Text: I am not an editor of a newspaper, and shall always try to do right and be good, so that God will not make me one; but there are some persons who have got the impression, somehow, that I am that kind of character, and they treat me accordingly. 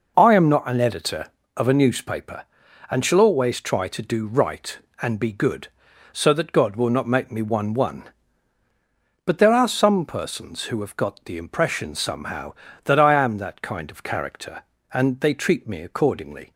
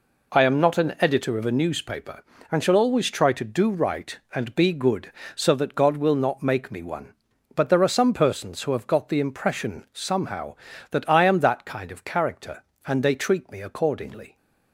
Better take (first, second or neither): second